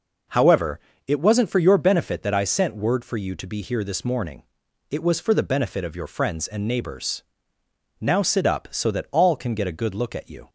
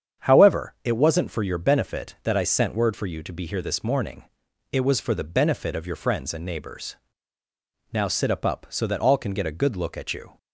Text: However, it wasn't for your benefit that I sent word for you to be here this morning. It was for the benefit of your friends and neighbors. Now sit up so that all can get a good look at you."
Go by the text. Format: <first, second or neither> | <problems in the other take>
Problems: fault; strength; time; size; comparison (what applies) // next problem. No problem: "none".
first | starts louder than the rest; strong; until 1.3 s; 8 dB // says "up" twice; at 8.4 s